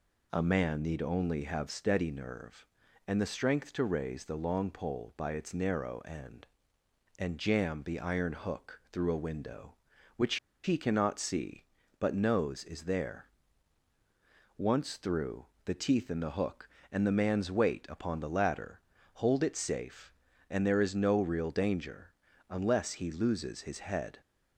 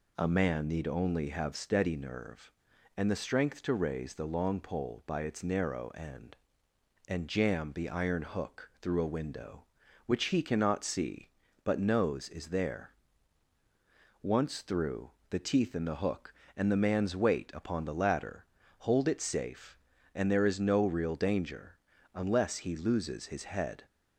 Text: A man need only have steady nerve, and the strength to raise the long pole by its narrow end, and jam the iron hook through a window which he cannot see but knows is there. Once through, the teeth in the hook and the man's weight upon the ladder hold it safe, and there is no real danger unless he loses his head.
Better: second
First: pauses between "which" and "he"; slight; at 10.3 s; 0.27 s long // pauses between "ladder" and "hold"; slight; at 18.7 s; 0.36 s long // pauses between "danger" and "unless"; slight; at 22.1 s; 0.36 s long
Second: pauses between "ladder" and "hold"; slight; at 18.4 s; 0.36 s long // pauses between "danger" and "unless"; slight; at 21.7 s; 0.36 s long

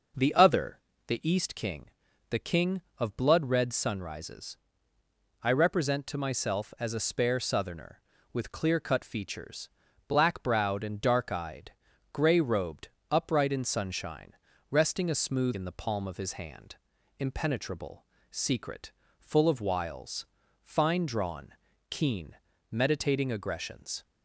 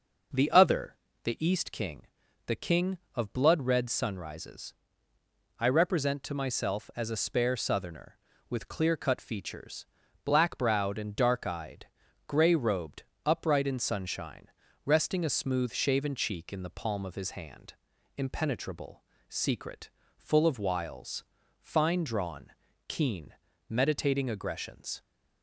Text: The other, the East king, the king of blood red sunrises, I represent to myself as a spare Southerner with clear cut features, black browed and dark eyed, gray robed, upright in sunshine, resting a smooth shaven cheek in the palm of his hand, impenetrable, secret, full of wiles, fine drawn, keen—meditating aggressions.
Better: second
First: skips "shaven cheek"; at 15.5 s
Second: none

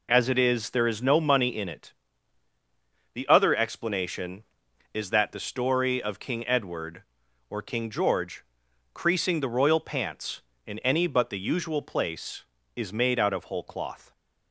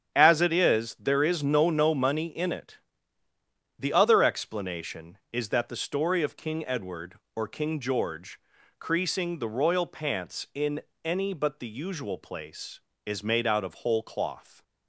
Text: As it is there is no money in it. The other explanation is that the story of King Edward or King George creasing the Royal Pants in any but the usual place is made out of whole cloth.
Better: first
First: pauses between "George" and "creasing"; noticeable; at 8.4 s; 0.48 s long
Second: starts louder than the rest; strong; until 1.1 s; 8 dB // says "no" twice; at 1.7 s // pauses between "George" and "creasing"; at 8.3 s; 0.42 s long // pauses between "in" and "any"; slight; at 10.8 s; 0.24 s long

